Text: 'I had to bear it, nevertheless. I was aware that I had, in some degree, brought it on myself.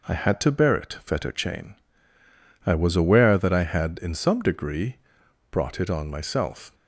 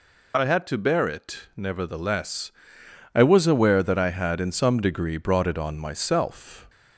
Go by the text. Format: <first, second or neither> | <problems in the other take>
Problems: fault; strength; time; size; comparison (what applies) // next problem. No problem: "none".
second | says "fetterchain" for "nevertheless"; at 1.0 s